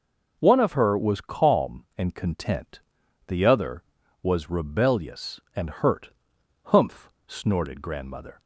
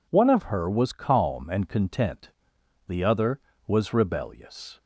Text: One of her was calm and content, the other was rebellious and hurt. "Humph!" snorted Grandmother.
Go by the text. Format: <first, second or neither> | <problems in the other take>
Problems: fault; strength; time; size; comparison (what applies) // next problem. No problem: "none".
first | stops before "and hurt Humph snorted Grandmother"; at 4.7 s